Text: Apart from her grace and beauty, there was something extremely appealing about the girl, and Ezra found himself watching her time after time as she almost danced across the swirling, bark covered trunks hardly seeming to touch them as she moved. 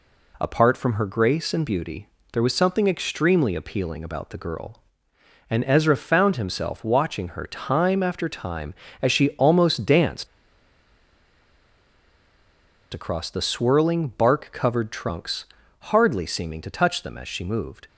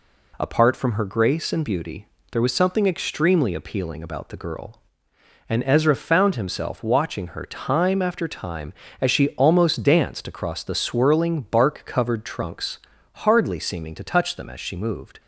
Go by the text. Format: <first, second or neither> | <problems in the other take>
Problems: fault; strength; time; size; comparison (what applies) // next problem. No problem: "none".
second | pauses between "danced" and "across"; strong; at 10.2 s; 2.6 s long // pauses between "trunks" and "hardly"; at 15.4 s; 0.38 s long; also in the second